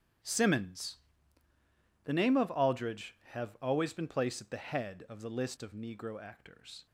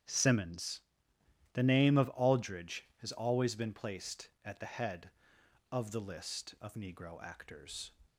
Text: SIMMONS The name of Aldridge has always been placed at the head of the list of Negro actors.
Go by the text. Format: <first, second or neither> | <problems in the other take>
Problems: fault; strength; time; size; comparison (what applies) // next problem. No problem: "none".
second | starts louder than the rest; strong; until 2.3 s; 9 dB; strong in the second // pauses between "SIMMONS" and "The"; at 0.9 s; 1.0 s long; noticeable in the second // says "have" for "has"; at 3.3 s